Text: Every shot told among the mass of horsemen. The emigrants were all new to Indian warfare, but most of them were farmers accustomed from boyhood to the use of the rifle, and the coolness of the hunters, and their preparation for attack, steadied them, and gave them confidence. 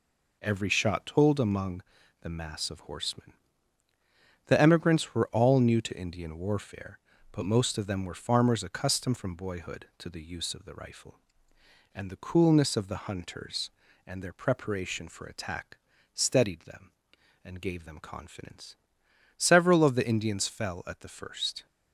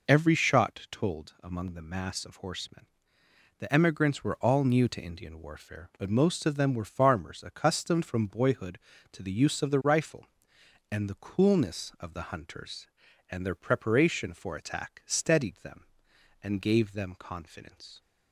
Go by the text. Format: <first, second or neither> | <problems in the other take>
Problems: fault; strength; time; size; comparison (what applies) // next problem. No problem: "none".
second | pauses between "among" and "the"; at 1.8 s; 0.40 s long // goes on to say "Several of the Indians fell at the first"; strong; from 19.3 s on; 2.2 s long